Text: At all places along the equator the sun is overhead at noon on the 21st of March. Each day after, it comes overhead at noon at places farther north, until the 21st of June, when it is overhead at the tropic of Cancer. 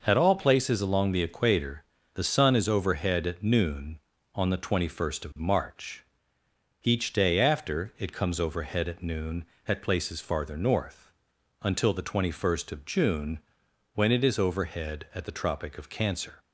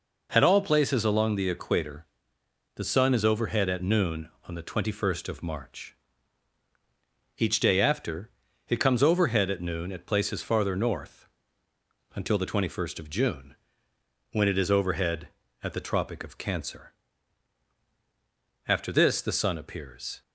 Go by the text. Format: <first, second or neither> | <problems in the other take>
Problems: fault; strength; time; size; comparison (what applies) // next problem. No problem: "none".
first | pauses between "equator" and "the"; noticeable; at 2.0 s; 0.70 s long; slight in the first // goes on to say "After this the sun appears"; from 18.6 s on; 1.5 s long